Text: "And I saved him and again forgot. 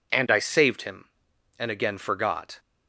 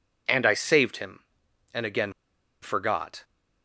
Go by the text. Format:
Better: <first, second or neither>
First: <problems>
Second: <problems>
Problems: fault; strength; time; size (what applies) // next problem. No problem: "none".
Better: first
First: none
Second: pauses between "again" and "forgot"; noticeable; at 2.1 s; 0.49 s long